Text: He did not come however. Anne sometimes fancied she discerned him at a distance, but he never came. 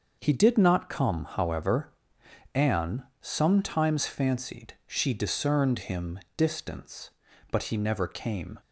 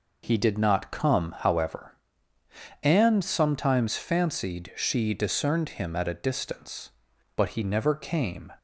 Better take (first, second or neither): second